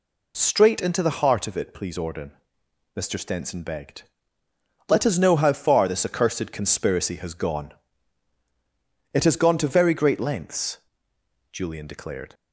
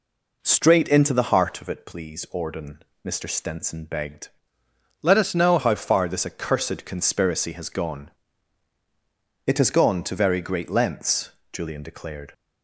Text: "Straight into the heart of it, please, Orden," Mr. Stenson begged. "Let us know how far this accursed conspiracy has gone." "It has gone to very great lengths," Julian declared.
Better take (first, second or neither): first